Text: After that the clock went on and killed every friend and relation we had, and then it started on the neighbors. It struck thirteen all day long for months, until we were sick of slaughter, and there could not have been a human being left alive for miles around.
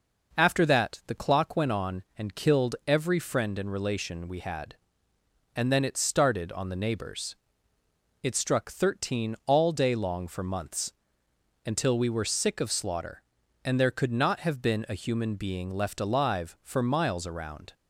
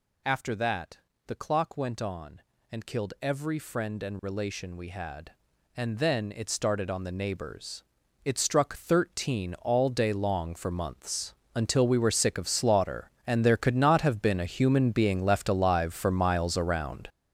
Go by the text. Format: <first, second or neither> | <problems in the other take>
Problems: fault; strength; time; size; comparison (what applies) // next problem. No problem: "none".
first | gets louder; strong; throughout; 10.5 dB // pauses between "that" and "the"; slight; at 0.9 s; 0.30 s long